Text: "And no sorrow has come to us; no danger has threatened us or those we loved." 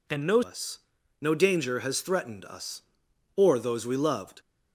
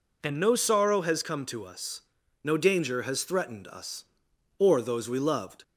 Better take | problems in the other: second | skips "sorrow has come to"; at 0.4 s

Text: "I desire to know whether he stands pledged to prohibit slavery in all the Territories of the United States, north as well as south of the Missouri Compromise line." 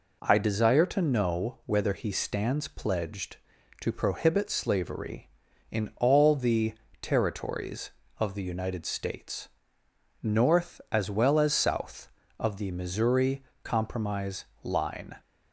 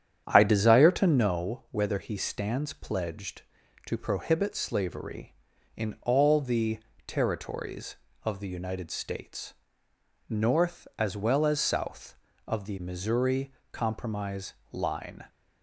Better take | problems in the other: first | starts louder than the rest; strong; until 1.3 s; 9.5 dB // pauses between "the" and "Territories"; slight; at 6.7 s; 0.26 s long; slight in the first // pauses between "Missouri" and "Compromise"; slight; at 13.5 s; 0.18 s long; slight in the first // pauses between "Compromise" and "line"; slight; at 14.5 s; 0.18 s long; slight in the first

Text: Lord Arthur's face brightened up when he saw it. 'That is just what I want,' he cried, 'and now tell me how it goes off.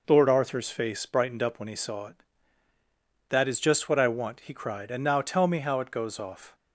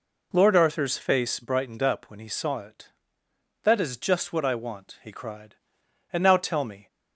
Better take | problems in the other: first | stops before "how it goes off"; at 6.8 s

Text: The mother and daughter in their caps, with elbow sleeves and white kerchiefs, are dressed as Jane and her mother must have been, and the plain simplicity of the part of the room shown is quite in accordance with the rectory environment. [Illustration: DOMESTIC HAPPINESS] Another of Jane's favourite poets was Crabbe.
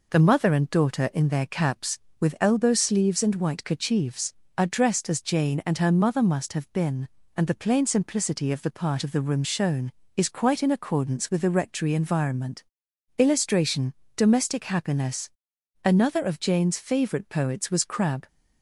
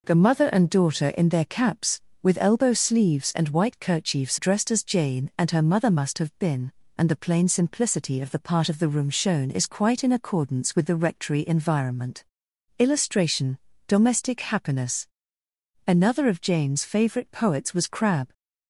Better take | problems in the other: first | skips "are"; at 4.3 s // pauses between "HAPPINESS" and "Another"; noticeable; at 15.0 s; 0.80 s long; noticeable in the first

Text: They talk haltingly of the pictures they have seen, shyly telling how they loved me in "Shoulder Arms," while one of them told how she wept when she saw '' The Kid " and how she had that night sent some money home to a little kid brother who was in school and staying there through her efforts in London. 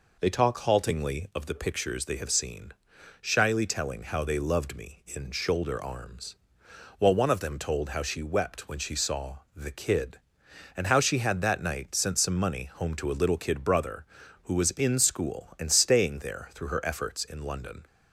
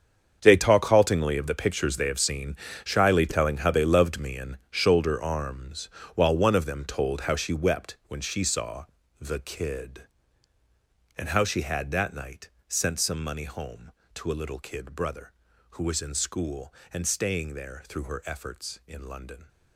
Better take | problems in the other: first | gets quieter; strong; throughout; 14.5 dB // pauses between "night" and "sent"; slight; at 12.4 s; 0.22 s long

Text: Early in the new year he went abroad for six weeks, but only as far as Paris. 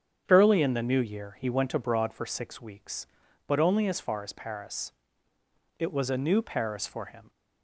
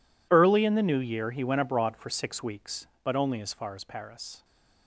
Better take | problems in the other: second | starts louder than the rest; strong; until 1.2 s; 8 dB // goes on to say "It was a new Paris for him"; from 5.7 s on; 1.5 s long

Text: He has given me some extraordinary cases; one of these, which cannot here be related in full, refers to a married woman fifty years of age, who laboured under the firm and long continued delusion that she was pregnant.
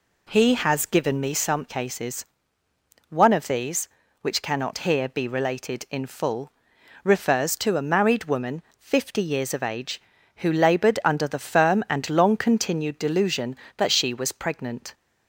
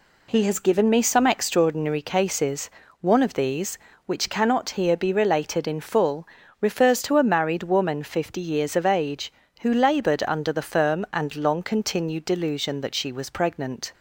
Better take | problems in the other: second | skips "extraordinary"; at 1.6 s // pauses between "woman" and "fifty"; slight; at 8.6 s; 0.16 s long

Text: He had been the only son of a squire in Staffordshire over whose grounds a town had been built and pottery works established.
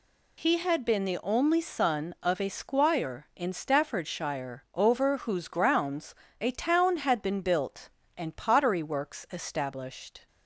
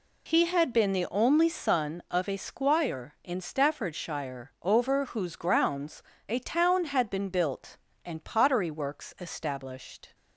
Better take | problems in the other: first | starts louder than the rest; slight; until 1.8 s; 2 dB // pauses between "grounds" and "a"; slight; at 6.0 s; 0.24 s long; slight in the first

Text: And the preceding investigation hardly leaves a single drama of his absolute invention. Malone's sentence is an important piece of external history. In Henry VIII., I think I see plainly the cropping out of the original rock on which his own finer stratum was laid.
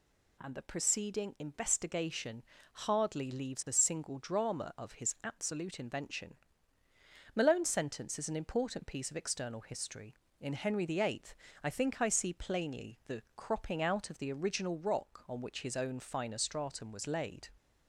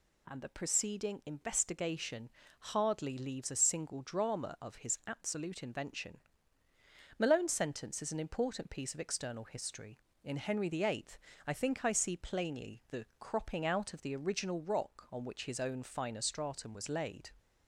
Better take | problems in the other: neither | pauses between "investigation" and "hardly"; slight; the same in both

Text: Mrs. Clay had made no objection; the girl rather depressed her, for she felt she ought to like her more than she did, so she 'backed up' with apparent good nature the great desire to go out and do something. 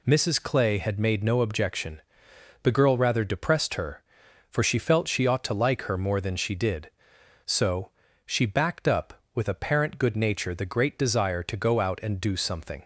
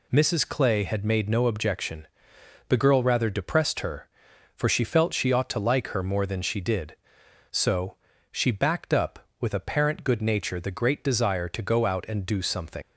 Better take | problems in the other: first | pauses between "so" and "she"; slight; at 7.9 s; 0.34 s long; slight in the first // leaves "something" unfinished; at 12.8 s; 70 ms

